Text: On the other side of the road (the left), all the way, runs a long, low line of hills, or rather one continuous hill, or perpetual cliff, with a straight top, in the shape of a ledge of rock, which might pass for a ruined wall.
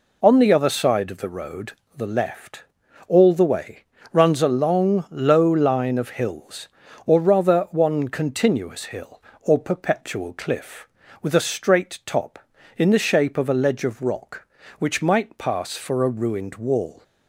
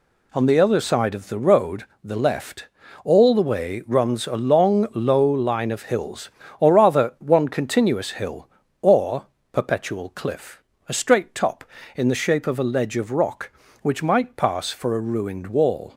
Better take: first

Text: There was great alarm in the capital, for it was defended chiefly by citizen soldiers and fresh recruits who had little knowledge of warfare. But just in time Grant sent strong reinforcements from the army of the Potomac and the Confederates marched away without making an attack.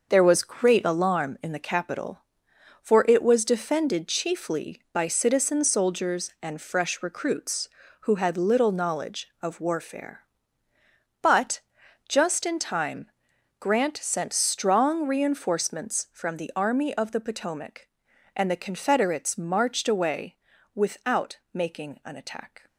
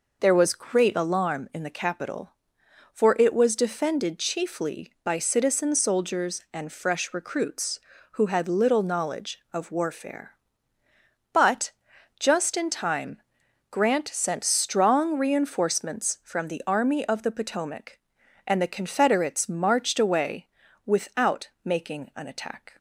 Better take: second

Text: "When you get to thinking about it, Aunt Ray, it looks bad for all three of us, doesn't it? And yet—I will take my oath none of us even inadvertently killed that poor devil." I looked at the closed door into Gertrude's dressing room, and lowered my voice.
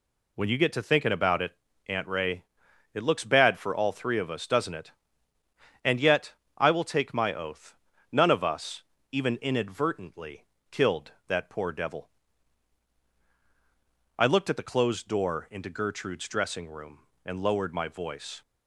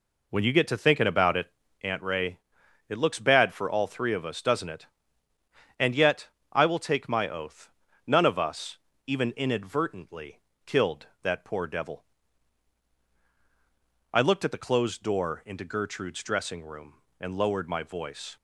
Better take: first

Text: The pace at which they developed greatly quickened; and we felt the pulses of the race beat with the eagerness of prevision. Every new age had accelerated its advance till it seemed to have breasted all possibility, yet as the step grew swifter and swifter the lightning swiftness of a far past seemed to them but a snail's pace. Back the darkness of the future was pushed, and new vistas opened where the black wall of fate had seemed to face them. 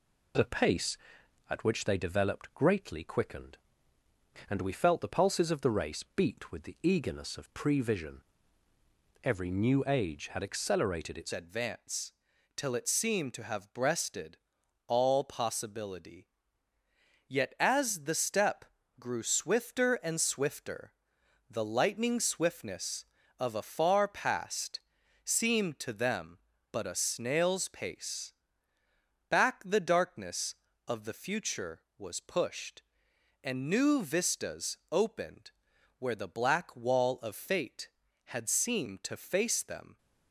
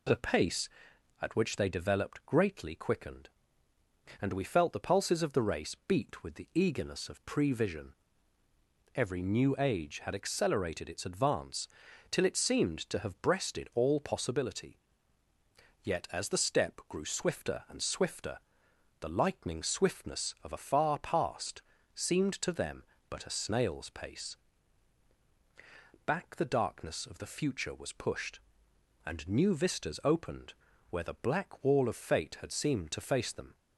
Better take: second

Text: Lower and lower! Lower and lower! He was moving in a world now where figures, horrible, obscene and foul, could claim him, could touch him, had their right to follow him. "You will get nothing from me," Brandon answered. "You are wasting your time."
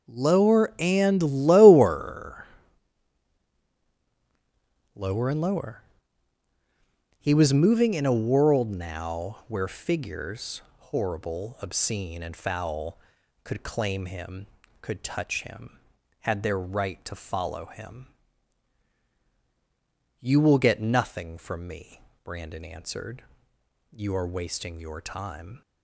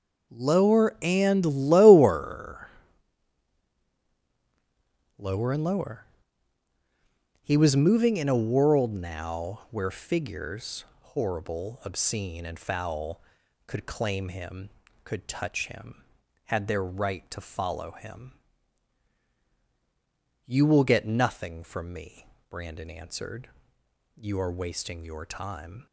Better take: neither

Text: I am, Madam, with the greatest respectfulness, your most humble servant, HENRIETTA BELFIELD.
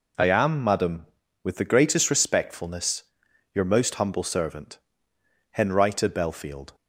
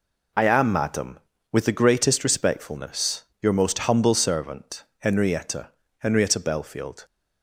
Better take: first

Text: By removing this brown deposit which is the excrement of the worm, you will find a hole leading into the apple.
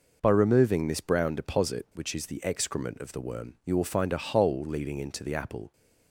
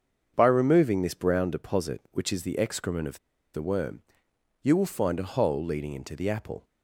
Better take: first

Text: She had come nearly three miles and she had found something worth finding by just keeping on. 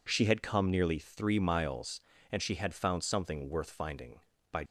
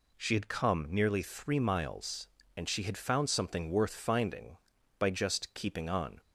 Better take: second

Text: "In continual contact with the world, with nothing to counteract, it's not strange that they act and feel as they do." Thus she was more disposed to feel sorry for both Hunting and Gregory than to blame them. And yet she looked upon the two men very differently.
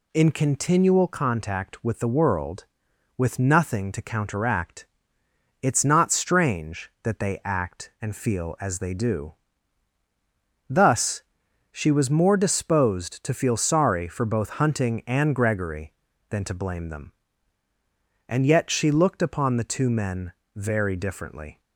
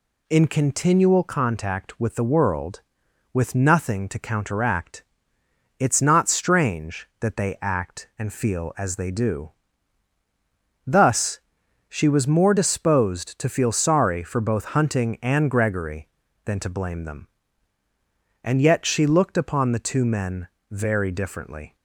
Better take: neither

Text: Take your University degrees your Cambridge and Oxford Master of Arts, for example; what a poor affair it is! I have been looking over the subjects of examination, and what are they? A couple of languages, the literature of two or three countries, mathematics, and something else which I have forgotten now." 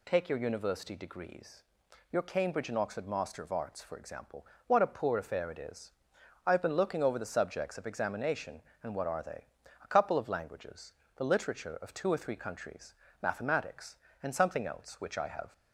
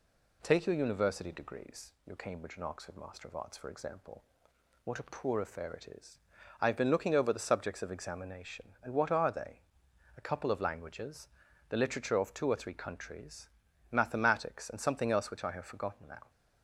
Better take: second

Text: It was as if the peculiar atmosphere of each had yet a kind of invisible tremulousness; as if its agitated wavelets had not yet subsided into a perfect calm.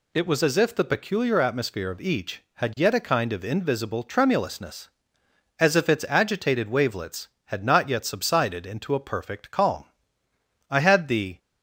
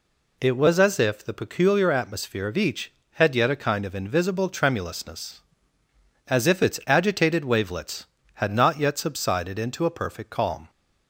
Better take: second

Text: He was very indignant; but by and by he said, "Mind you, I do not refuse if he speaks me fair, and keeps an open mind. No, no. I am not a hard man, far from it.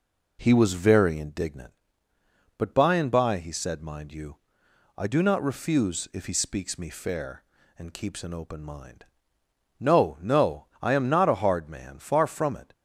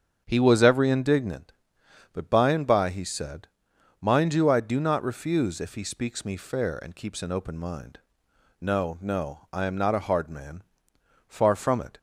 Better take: first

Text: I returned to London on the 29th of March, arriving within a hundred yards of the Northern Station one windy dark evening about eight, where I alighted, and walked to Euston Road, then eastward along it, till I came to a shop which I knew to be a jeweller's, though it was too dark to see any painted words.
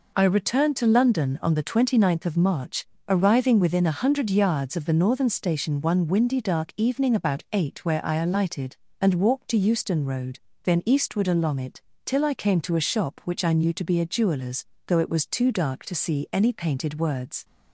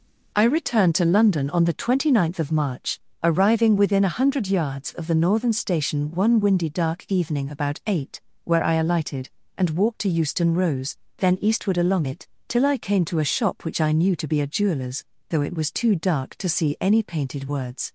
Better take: first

